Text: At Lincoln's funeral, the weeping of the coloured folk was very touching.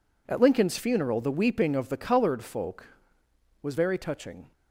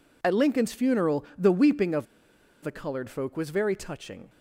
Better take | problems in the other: first | pauses between "of" and "the"; noticeable; at 2.0 s; 0.57 s long

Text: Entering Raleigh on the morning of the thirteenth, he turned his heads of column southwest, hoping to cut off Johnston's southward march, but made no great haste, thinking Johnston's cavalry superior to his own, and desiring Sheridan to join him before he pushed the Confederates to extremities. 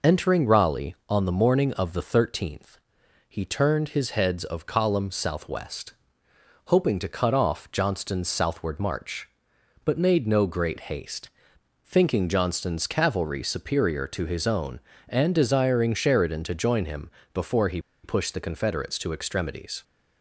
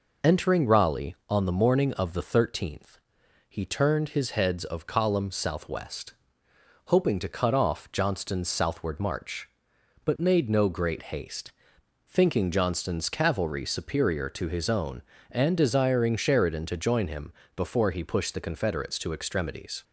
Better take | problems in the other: second | pauses between "him" and "before"; slight; at 17.1 s; 0.24 s long; slight in the second // pauses between "he" and "pushed"; slight; at 17.7 s; 0.24 s long

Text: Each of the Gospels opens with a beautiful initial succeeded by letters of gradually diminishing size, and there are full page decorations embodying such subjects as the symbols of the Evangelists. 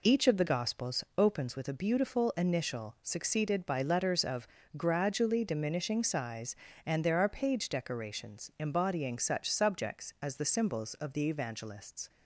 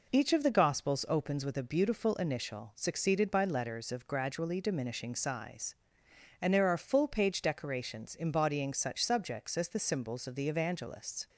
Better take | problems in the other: second | pauses between "of" and "gradually"; slight; at 4.4 s; 0.28 s long // skips "full"; at 7.2 s

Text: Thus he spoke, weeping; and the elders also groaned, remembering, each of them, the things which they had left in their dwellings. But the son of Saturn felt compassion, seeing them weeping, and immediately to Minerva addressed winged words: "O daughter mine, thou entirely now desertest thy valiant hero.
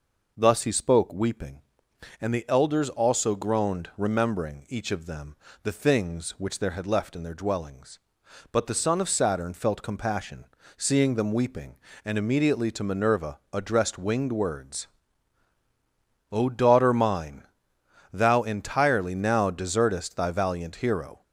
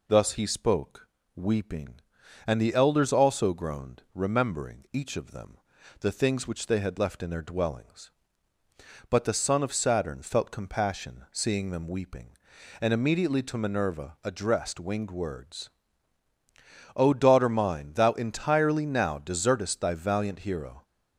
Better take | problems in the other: second | says "there" for "they"; at 6.5 s

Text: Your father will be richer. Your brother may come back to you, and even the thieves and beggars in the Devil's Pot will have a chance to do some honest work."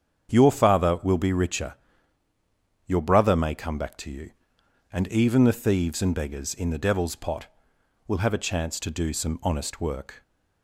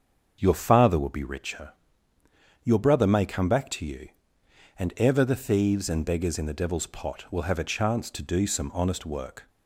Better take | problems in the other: first | starts louder than the rest; until 1.4 s; 7 dB; strong in the first // says "ever" for "even"; at 4.9 s

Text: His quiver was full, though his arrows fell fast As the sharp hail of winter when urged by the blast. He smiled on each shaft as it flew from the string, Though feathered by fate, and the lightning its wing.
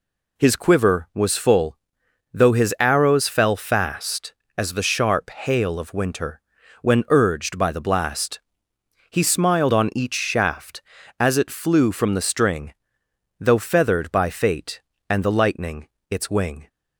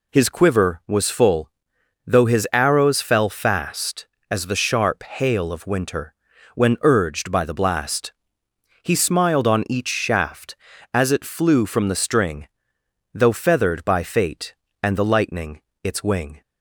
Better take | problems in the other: neither | pauses between "winter" and "when"; the same in both // pauses between "lightning" and "its"; slight; the same in both

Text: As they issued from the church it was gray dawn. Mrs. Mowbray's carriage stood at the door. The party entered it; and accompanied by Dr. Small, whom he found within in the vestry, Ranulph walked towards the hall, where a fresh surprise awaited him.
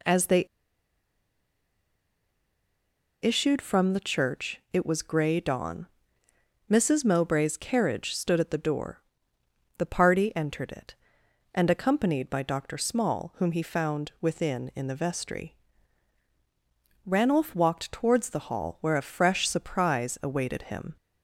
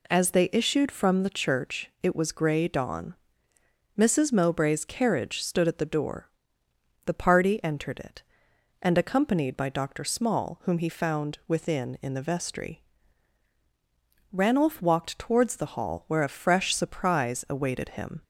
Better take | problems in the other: second | pauses between "they" and "issued"; strong; at 0.4 s; 2.7 s long

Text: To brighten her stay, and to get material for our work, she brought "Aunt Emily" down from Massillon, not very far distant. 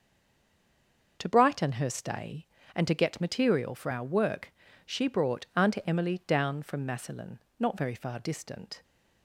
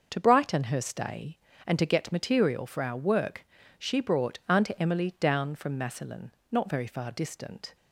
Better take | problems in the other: second | stays silent before the first word; noticeable; until 1.1 s; 1.1 s long // starts louder than the rest; noticeable; until 2.2 s; 6 dB; noticeable in the second

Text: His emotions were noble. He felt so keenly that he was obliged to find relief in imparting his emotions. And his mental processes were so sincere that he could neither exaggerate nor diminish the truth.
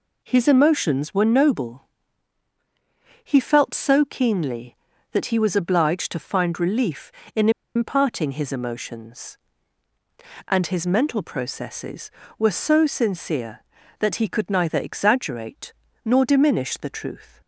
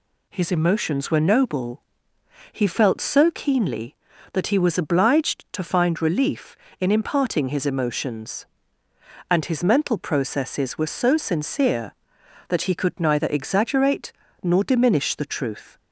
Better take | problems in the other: second | pauses between "in" and "imparting"; slight; at 7.4 s; 0.26 s long // pauses between "exaggerate" and "nor"; slight; at 15.7 s; 0.32 s long; slight in the second

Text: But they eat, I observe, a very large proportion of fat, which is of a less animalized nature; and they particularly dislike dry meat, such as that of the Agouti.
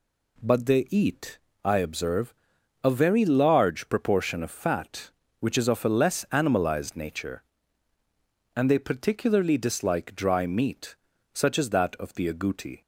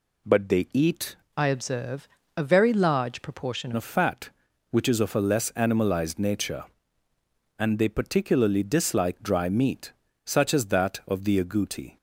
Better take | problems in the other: first | changes voice from "I" to "proportion"; from 1.3 to 3.7 s; 2.4 s long

